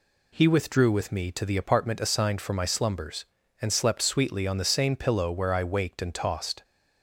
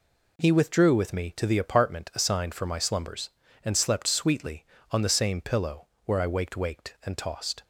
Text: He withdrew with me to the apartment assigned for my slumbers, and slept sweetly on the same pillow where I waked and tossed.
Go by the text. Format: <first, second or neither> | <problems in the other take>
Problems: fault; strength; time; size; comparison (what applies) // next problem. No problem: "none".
first | pauses between "pillow" and "where"; slight; at 5.8 s; 0.20 s long // says "waked" twice; at 6.5 s